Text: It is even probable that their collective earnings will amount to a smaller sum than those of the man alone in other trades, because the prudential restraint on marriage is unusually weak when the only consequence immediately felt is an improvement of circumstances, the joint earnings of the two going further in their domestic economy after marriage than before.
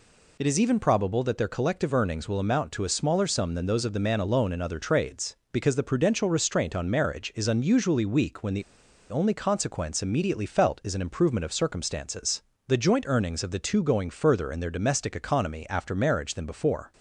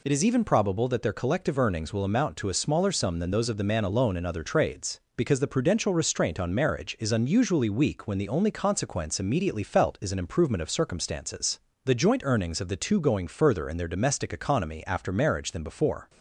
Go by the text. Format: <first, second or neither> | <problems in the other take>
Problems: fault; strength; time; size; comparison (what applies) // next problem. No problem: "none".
second | pauses between "the" and "only"; noticeable; at 8.6 s; 0.47 s long